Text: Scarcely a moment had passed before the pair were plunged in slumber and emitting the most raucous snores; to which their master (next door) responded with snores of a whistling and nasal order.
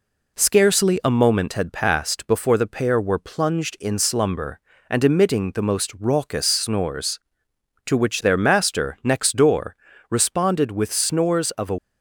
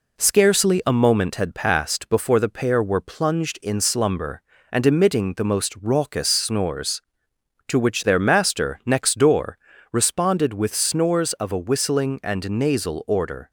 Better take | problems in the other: second | stops before "whistling and nasal order"; at 11.7 s

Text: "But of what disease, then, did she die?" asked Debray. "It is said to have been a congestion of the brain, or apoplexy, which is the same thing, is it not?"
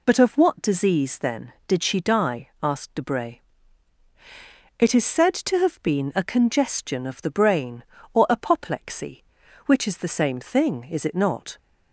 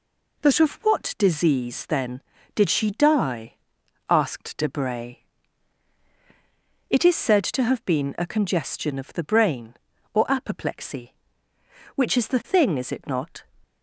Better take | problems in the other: first | skips "same"; at 12.4 s

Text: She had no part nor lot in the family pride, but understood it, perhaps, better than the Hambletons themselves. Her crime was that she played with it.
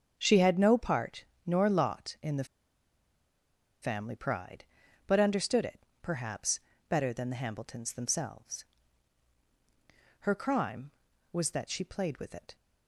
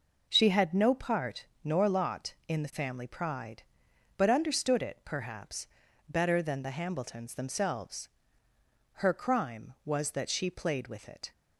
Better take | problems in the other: second | starts louder than the rest; strong; until 1.1 s; 7.5 dB // pauses between "part" and "nor"; slight; at 1.2 s; 0.20 s long; slight in the second // pauses between "the" and "family"; strong; at 2.4 s; 1.3 s long

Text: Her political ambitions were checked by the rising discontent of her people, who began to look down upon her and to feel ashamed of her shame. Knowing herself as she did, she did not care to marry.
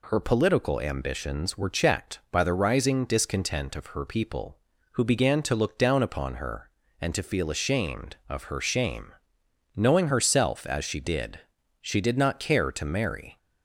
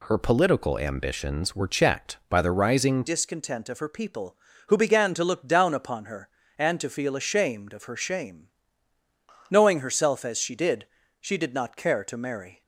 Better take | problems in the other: first | changes voice at "discontent"; from 3.0 s on; 9.6 s long

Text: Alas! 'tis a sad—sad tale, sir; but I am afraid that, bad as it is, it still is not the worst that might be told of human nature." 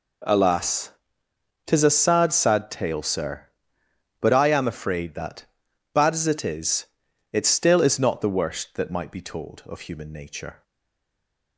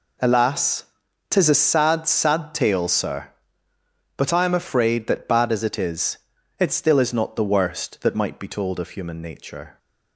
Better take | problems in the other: second | stays silent after the last word; from 10.6 s on; 0.9 s long

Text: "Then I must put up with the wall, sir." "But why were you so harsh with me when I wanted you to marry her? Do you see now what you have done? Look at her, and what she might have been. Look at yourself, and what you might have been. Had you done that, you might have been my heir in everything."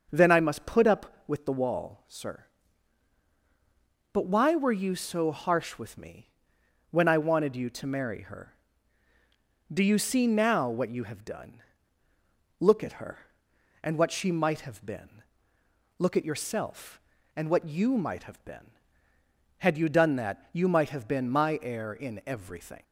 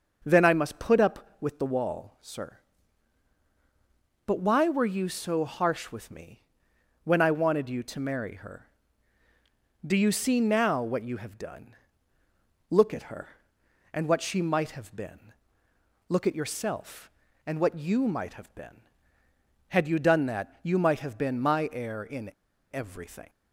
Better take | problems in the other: first | pauses between "me" and "when"; noticeable; at 6.4 s; 0.60 s long; noticeable in the first // pauses between "in" and "everything"; at 22.3 s; 0.42 s long

